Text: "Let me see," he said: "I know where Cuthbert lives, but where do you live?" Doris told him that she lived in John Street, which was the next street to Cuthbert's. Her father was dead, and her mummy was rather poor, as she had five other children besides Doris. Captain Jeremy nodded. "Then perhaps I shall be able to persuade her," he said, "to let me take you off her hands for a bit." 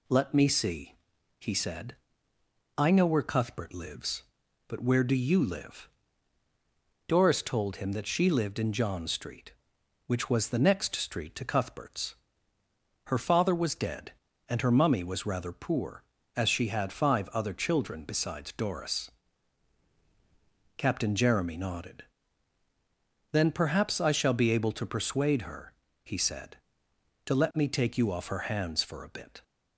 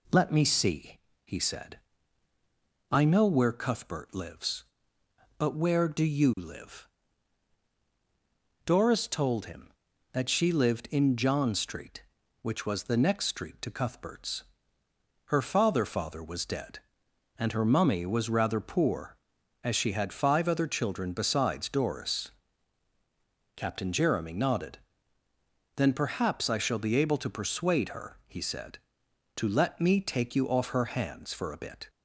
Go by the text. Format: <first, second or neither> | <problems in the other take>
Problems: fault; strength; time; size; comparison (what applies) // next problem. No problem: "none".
first | says "father" twice; at 15.8 s